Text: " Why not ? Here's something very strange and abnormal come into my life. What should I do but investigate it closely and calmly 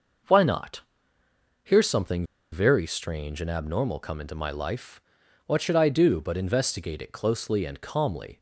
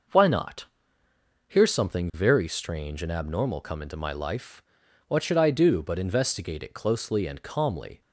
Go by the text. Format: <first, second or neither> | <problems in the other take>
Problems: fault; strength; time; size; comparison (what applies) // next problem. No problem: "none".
second | pauses between "something" and "very"; slight; at 2.2 s; 0.27 s long